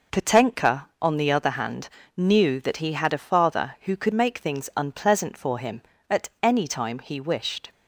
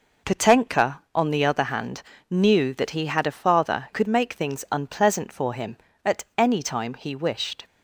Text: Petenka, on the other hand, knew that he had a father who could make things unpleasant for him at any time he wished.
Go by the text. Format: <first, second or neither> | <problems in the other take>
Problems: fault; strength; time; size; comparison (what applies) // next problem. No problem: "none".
first | skips "who"; at 3.9 s